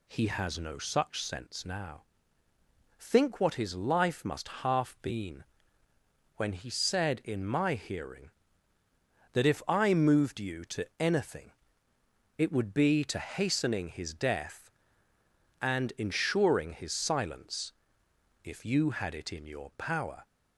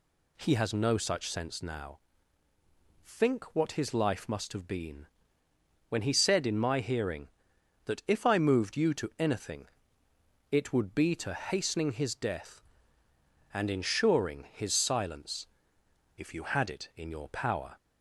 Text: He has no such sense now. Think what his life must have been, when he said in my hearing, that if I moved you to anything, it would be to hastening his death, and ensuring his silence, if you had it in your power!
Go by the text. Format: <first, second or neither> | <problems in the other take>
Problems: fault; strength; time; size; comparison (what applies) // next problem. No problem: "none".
second | says "half" for "have"; at 4.4 s